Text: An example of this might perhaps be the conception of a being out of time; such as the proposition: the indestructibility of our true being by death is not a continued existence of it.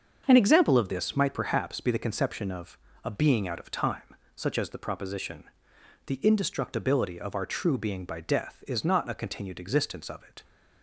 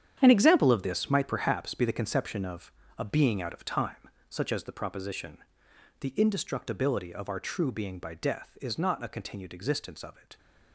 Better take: first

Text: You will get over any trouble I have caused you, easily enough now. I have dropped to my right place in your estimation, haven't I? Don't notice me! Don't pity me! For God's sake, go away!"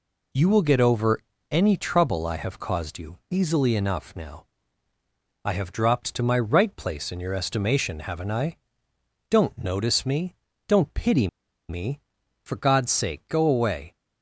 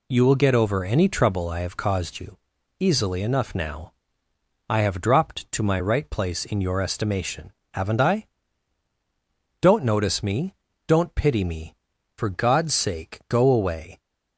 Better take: second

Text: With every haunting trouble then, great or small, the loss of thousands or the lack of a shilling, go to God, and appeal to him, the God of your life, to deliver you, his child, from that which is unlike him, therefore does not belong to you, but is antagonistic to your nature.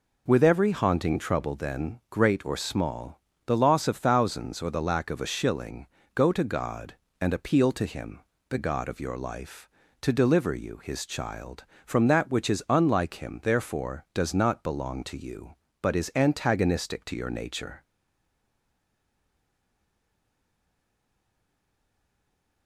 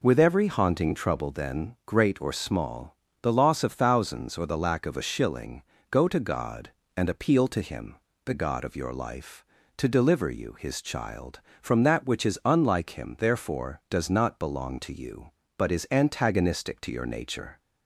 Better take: second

